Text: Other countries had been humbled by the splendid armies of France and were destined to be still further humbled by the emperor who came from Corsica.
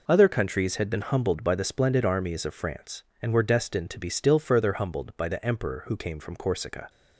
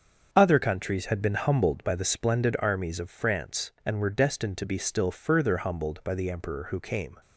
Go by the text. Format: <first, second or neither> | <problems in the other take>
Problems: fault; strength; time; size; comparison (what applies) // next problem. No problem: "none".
first | starts louder than the rest; until 1.3 s; 7 dB // stops before "from Corsica"; at 7.2 s